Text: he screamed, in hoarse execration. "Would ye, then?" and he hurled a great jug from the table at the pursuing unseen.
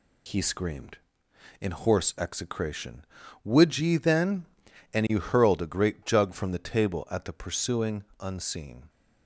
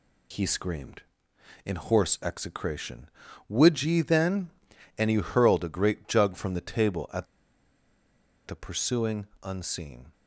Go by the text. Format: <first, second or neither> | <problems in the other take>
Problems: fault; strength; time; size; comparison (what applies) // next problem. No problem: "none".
first | pauses between "at" and "the"; at 7.2 s; 1.2 s long // pauses between "pursuing" and "unseen"; slight; at 9.2 s; 0.16 s long; slight in the first